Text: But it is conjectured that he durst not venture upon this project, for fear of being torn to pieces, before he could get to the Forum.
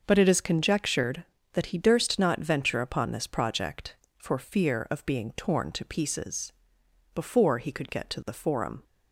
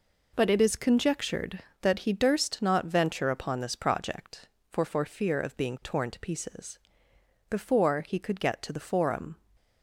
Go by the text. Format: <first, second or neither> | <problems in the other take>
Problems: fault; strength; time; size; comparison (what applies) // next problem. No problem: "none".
first | says "for" twice; at 4.8 s